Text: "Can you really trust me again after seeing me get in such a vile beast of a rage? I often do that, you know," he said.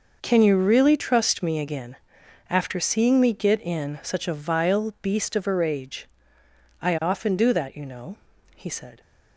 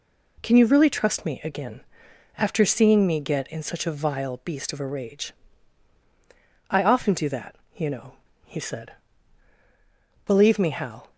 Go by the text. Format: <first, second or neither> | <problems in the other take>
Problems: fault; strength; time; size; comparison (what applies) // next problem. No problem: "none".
first | pauses between "again" and "after"; noticeable; at 1.8 s; 0.56 s long; noticeable in the first // goes on to say "Believe me Hal"; noticeable; from 10.2 s on; 0.86 s long